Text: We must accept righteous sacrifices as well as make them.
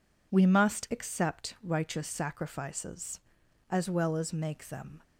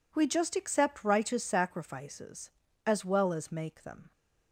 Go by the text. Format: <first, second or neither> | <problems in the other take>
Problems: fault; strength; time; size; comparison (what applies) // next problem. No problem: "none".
first | says "just" for "must"; at 0.2 s